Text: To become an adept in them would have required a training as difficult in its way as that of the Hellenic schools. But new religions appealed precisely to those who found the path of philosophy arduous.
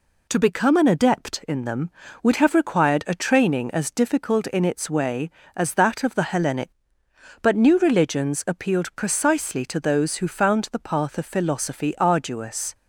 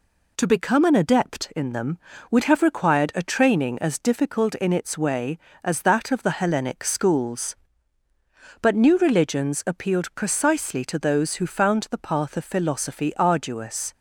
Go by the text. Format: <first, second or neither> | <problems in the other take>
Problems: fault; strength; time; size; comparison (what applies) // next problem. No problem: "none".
second | skips "schools"; at 7.0 s